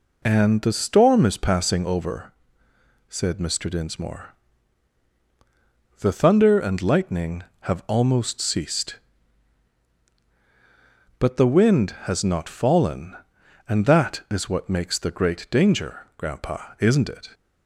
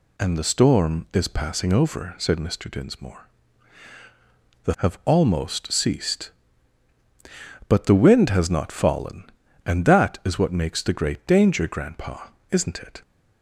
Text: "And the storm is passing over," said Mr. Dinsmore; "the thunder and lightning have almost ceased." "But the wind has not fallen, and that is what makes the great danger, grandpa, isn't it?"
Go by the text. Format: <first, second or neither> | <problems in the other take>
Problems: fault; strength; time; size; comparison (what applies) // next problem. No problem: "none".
first | skips "thunder and lightning"; at 4.7 s